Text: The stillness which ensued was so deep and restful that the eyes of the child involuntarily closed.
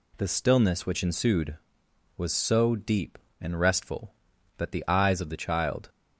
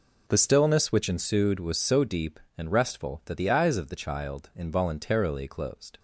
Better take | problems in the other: second | stops before "involuntarily closed"; at 5.8 s

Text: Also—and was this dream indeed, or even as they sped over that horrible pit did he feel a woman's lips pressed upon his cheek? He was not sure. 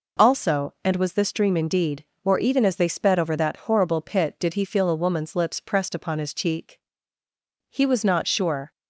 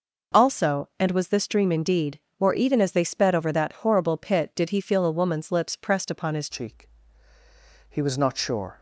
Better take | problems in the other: first | changes voice at "cheek"; from 6.4 s on; 2.3 s long

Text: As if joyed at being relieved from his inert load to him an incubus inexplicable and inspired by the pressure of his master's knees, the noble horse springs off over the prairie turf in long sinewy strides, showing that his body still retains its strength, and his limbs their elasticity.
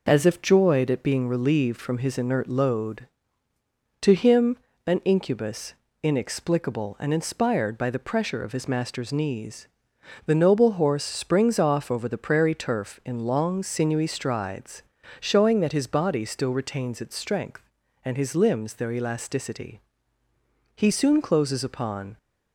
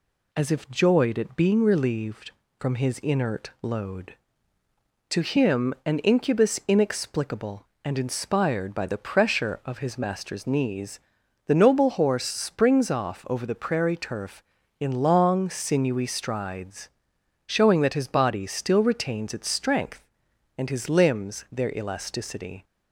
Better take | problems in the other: second | pauses between "him" and "an"; slight; at 4.5 s; 0.28 s long // pauses between "incubus" and "inexplicable"; slight; at 5.7 s; 0.28 s long // goes on to say "He soon closes upon"; from 20.7 s on; 1.4 s long

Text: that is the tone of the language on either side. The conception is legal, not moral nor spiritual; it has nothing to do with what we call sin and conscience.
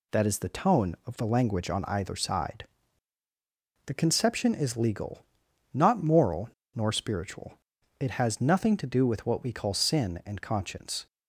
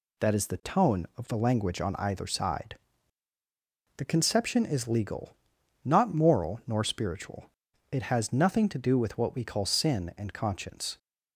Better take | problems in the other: second | pauses between "moral" and "nor"; slight; at 6.4 s; 0.25 s long

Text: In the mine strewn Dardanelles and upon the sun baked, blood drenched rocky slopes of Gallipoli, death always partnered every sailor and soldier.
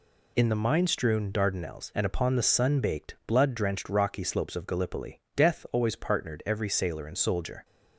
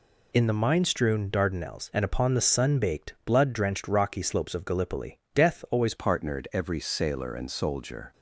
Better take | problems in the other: first | changes voice at "partnered"; from 5.9 s on; 2.2 s long

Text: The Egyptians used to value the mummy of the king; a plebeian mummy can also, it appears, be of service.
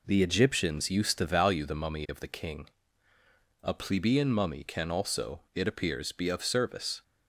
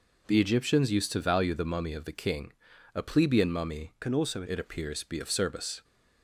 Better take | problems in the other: first | changes voice from "can" to "also"; from 3.9 to 4.4 s; 0.5 s long

